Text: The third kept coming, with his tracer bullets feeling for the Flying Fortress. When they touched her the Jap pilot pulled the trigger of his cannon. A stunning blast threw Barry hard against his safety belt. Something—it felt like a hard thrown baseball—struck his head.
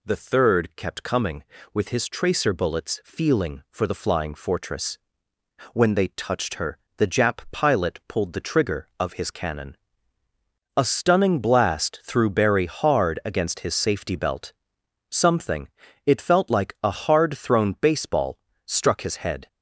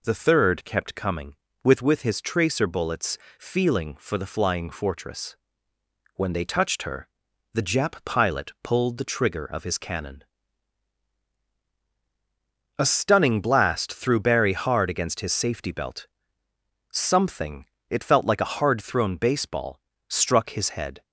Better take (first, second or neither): first